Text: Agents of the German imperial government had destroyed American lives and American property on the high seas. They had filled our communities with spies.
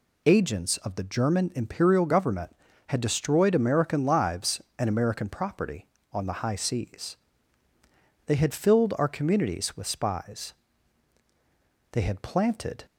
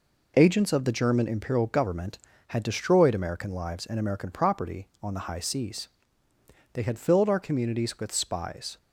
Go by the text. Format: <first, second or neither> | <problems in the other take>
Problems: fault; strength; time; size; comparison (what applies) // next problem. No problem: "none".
second | goes on to say "They had planted"; noticeable; from 11.9 s on; 0.94 s long